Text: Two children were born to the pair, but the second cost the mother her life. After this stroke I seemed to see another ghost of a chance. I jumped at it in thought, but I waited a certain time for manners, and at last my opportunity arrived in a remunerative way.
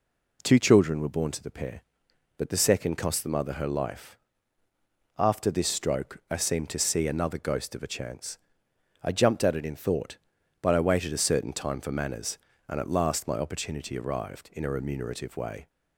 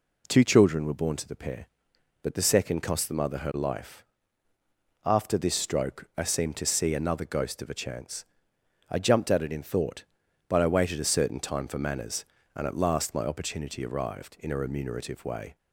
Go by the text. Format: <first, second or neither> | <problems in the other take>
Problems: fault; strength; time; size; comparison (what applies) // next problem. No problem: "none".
neither | none